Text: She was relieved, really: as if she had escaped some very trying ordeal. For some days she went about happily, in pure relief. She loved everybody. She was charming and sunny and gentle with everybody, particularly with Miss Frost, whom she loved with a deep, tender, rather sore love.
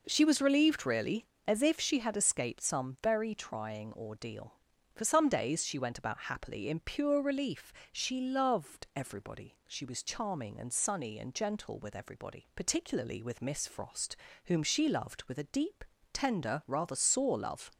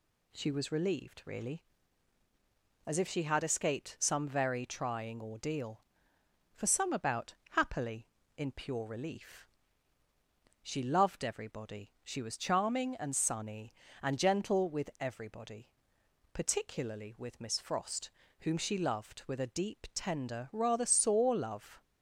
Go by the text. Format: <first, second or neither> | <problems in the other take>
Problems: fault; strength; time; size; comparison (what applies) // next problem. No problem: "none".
first | skips "days she went"; at 6.9 s // pauses between "about" and "happily"; slight; at 7.3 s; 0.16 s long